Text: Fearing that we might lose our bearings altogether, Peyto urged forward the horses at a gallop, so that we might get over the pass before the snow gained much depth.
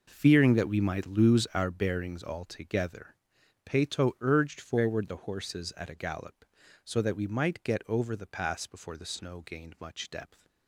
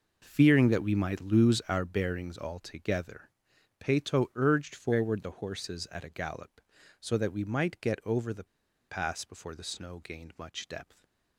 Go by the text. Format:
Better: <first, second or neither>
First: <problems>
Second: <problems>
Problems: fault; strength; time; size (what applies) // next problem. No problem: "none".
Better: first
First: none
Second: pauses between "the" and "pass"; at 8.4 s; 0.43 s long // stays silent after the last word; slight; from 10.8 s on; 0.5 s long